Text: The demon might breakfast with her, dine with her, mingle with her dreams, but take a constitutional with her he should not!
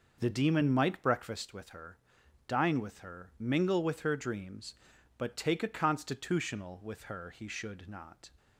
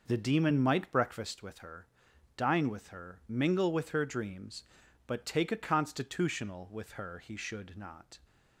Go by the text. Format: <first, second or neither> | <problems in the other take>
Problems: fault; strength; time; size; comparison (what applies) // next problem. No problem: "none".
neither | none